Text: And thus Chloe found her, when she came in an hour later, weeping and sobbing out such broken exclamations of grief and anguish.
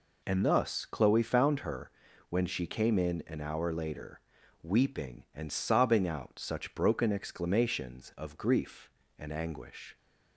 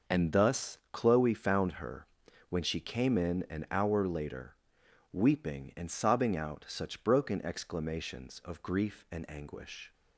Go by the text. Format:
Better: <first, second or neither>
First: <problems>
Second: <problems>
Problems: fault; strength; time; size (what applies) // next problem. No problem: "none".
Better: neither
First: none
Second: none